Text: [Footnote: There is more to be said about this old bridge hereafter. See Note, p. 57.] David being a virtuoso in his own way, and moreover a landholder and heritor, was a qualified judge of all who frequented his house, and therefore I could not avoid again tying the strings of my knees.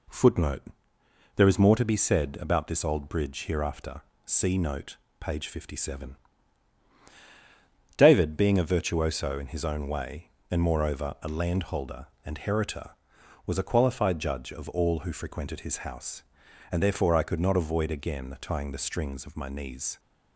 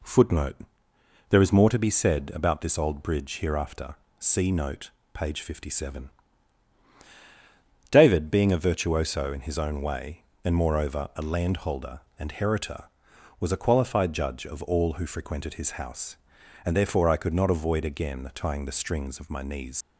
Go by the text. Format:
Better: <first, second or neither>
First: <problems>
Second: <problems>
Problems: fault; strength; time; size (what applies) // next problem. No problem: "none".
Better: first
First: none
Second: leaves "knees" unfinished; at 19.8 s; 120 ms